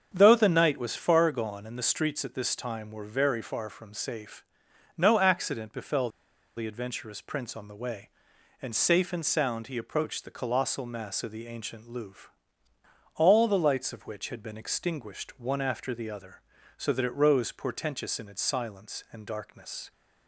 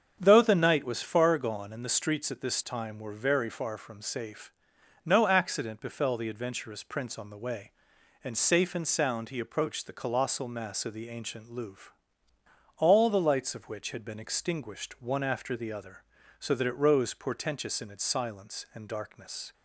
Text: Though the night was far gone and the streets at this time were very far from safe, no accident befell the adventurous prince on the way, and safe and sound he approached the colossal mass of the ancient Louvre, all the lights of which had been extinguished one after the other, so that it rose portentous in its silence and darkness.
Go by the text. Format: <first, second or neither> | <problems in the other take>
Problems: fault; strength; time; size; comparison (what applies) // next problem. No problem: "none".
second | starts louder than the rest; strong; until 1.1 s; 7.5 dB; strong in the second // pauses between "befell" and "the"; noticeable; at 6.1 s; 0.46 s long